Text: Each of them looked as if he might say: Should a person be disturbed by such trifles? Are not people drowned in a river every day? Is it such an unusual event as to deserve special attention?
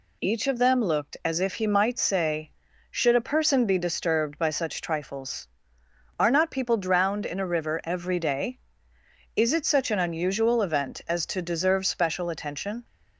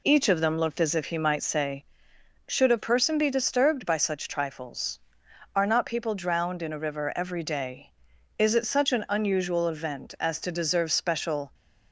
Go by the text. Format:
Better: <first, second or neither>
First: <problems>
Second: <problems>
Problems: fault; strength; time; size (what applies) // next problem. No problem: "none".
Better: first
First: none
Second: stops before "attention"; at 11.5 s